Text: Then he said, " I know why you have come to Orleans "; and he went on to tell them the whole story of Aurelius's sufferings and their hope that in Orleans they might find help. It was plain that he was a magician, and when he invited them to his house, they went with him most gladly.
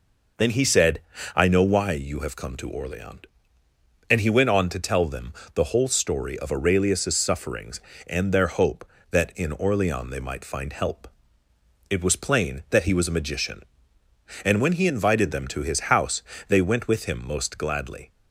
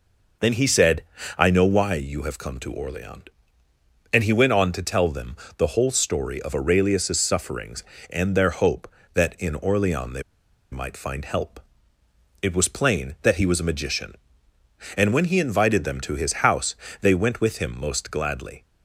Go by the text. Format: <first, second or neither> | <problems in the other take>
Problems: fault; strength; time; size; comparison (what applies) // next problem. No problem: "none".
first | pauses between "them" and "the"; slight; at 5.3 s; 0.22 s long; slight in the first // pauses between "they" and "might"; noticeable; at 10.2 s; 0.49 s long